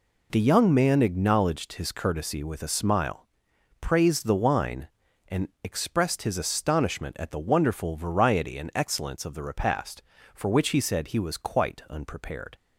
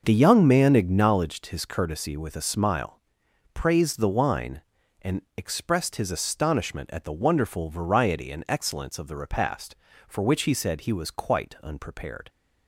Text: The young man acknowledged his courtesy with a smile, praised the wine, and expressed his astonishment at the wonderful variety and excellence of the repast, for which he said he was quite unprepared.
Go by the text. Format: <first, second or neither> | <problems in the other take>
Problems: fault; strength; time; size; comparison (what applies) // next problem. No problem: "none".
first | starts louder than the rest; noticeable; until 1.2 s; 6 dB